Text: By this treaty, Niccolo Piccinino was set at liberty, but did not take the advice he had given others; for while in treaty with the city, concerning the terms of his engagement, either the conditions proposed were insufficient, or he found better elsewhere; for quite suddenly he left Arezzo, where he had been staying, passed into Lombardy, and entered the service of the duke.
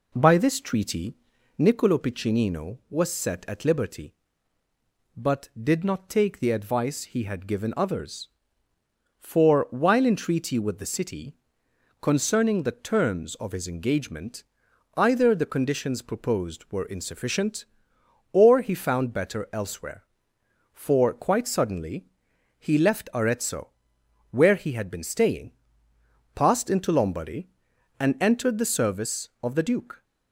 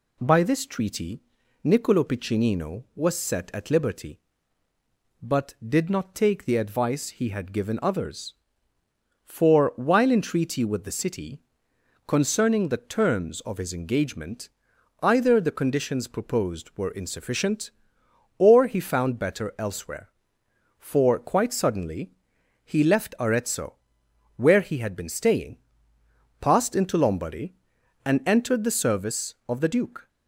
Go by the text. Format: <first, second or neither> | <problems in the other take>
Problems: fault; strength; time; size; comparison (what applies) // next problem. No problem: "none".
second | starts louder than the rest; slight; until 1.7 s; 3.5 dB // pauses between "suddenly" and "he"; noticeable; at 22.0 s; 0.54 s long; noticeable in the second